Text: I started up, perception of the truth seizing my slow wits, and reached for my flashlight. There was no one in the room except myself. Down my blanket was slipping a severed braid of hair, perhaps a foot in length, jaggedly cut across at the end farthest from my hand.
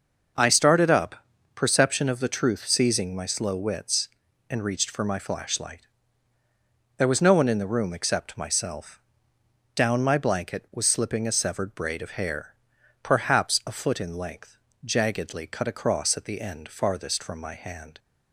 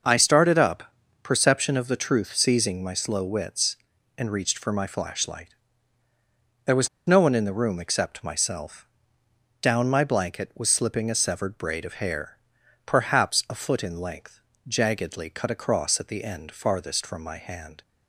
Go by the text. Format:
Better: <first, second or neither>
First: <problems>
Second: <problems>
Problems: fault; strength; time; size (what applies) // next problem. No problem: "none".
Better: first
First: none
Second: pauses between "was" and "no"; slight; at 6.8 s; 0.19 s long